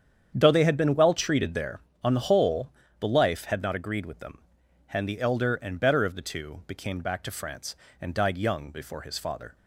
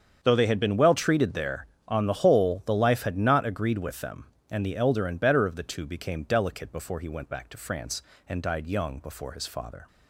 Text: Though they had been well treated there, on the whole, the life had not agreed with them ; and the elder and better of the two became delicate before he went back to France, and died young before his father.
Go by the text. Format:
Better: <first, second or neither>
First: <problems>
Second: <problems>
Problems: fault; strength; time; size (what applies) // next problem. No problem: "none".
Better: second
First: starts louder than the rest; strong; until 1.3 s; 8.5 dB // skips "delicate before he went"; at 7.0 s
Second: starts louder than the rest; strong; until 1.2 s; 7.5 dB